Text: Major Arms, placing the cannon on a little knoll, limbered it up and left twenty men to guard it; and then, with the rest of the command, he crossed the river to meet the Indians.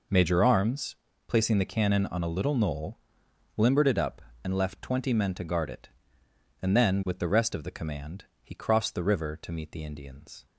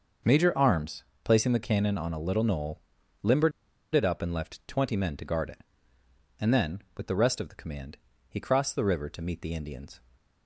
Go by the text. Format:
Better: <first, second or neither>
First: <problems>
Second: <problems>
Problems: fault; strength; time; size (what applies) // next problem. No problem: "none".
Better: first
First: none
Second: starts louder than the rest; until 1.4 s; 6 dB // pauses between "limbered" and "it"; at 3.5 s; 0.42 s long